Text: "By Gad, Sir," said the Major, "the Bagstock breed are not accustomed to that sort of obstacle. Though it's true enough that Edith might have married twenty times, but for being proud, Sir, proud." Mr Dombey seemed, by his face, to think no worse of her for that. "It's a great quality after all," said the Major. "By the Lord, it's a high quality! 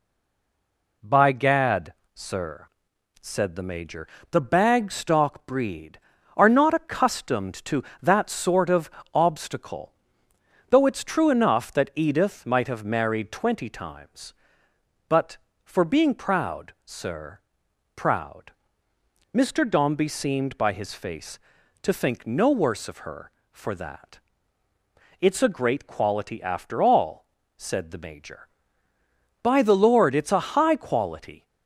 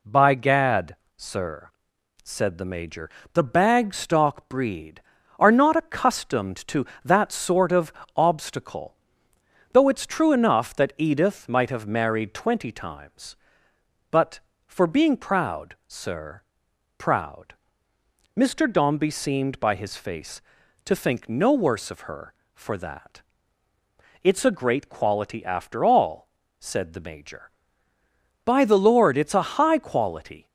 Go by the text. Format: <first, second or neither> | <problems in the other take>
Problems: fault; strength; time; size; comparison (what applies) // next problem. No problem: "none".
second | stays silent before the first word; until 1.0 s; 1.0 s long // pauses between "of" and "obstacle"; slight; at 8.8 s; 0.24 s long; slight in the second